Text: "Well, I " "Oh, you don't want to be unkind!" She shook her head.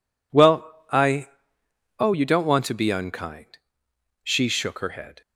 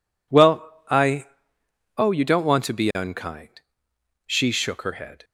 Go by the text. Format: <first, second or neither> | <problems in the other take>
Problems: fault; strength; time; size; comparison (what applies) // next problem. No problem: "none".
neither | none